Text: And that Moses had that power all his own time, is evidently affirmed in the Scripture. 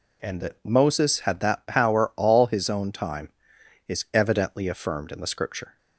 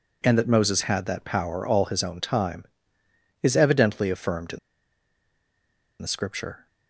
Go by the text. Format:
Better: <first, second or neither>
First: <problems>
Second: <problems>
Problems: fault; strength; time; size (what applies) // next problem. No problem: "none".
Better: first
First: none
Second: pauses between "in" and "the"; strong; at 4.5 s; 1.4 s long